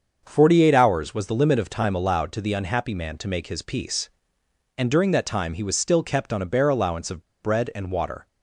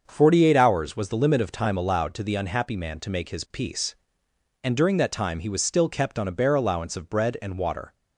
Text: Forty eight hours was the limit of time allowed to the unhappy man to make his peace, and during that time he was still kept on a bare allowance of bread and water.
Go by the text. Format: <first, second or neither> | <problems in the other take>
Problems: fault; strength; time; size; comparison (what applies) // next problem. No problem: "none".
second | starts louder than the rest; until 1.2 s; 6.5 dB; also in the second // pauses between "of" and "bread"; slight; at 7.2 s; 0.19 s long